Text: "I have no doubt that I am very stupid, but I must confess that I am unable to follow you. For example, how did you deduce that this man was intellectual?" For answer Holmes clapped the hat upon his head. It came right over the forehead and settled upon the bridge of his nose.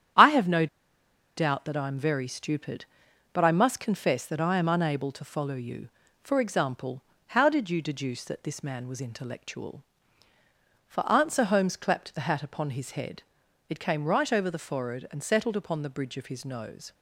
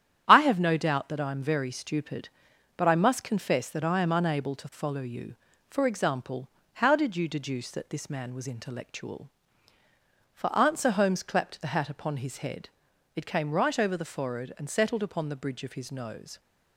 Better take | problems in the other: second | starts louder than the rest; strong; until 1.8 s; 10 dB; strong in the second // pauses between "no" and "doubt"; noticeable; at 0.6 s; 0.70 s long

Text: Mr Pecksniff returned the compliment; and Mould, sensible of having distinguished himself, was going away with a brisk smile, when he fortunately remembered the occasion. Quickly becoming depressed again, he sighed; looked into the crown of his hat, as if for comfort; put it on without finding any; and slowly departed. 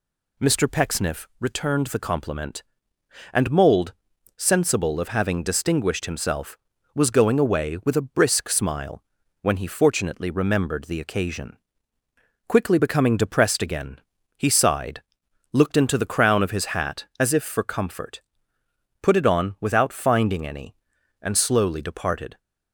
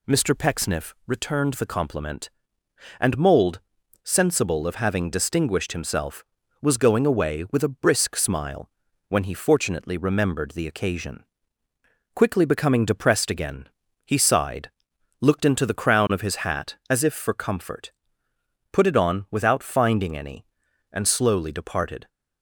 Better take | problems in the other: neither | none

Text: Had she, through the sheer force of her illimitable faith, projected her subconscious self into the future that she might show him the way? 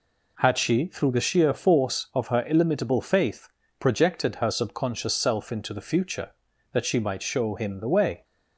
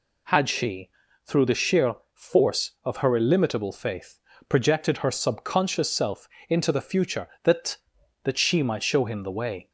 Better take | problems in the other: first | pauses between "sheer" and "force"; slight; at 1.9 s; 0.18 s long // pauses between "self" and "into"; slight; at 6.2 s; 0.22 s long // says "that" twice; at 8.2 s

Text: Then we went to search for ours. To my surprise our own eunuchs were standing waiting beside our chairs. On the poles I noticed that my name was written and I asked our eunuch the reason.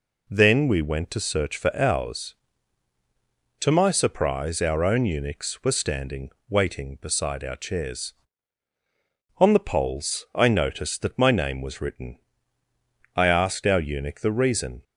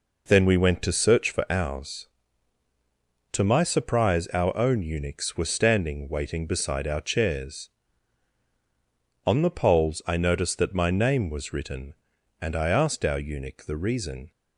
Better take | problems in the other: second | pauses between "standing" and "waiting"; slight; at 6.2 s; 0.20 s long // skips "and"; at 12.6 s

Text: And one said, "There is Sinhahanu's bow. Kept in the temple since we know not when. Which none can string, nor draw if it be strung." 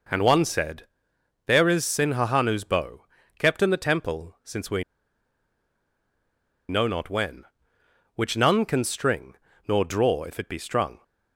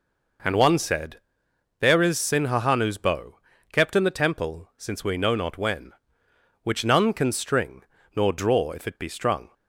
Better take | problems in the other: second | pauses between "we" and "know"; strong; at 4.8 s; 1.8 s long

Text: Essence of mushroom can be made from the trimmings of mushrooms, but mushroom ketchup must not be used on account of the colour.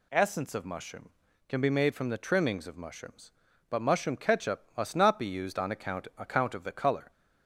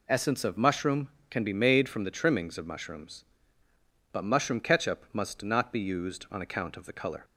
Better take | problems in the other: second | says "account" twice; at 6.1 s

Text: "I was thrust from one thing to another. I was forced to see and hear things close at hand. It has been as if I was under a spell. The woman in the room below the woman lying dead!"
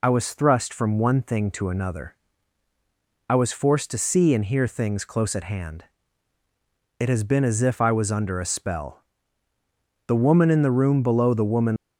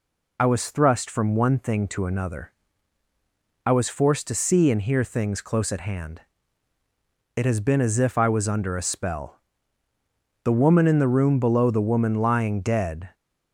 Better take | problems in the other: second | stops before "lying dead"; at 11.7 s

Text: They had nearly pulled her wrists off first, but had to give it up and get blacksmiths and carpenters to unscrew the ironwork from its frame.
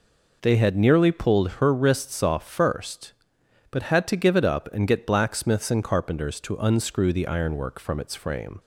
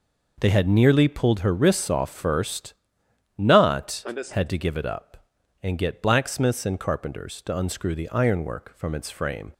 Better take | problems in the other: first | says "not" for "but"; at 3.3 s

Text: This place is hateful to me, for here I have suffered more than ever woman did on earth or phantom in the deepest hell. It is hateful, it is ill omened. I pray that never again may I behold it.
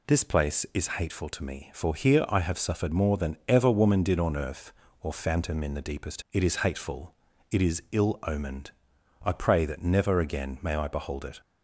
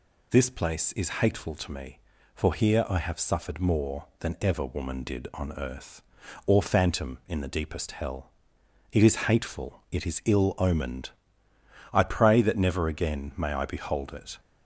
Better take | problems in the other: second | skips "hell"; at 6.2 s

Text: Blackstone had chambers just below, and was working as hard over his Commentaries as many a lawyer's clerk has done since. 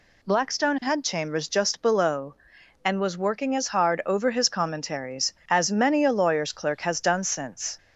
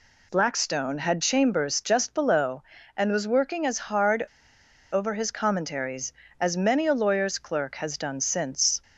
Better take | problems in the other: first | pauses between "hard" and "over"; noticeable; at 4.2 s; 0.69 s long

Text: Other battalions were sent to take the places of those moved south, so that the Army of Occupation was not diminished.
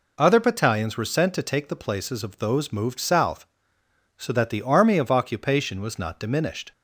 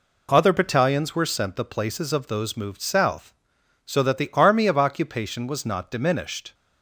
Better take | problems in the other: first | skips "to take"; at 1.5 s

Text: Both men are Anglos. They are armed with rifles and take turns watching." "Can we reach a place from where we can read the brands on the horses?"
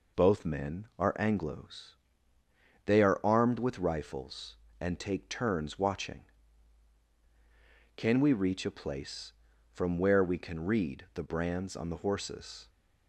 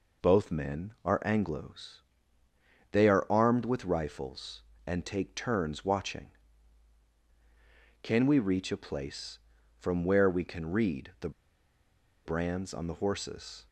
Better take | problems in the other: first | pauses between "the" and "brands"; noticeable; at 11.3 s; 0.95 s long

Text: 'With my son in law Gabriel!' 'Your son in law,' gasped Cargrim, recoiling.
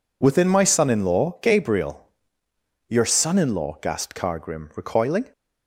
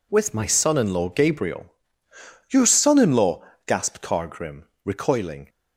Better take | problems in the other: second | says "Within" for "With"; at 0.2 s

